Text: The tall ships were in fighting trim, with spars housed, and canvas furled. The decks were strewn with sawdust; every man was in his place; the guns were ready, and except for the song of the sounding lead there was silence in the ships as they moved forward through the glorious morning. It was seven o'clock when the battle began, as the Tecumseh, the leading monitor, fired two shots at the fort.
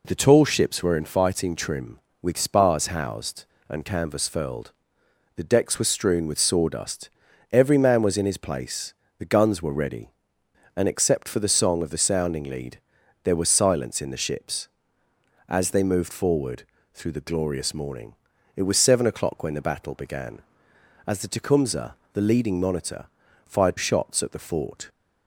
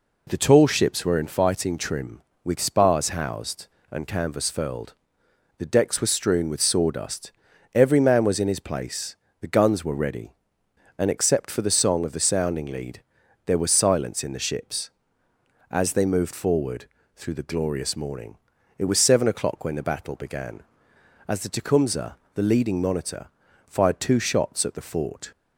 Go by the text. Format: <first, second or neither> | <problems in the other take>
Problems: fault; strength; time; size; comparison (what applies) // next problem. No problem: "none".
second | pauses between "lead" and "there"; at 12.7 s; 0.44 s long; also in the second // pauses between "forward" and "through"; slight; at 16.6 s; 0.32 s long; slight in the second // skips "two"; at 23.7 s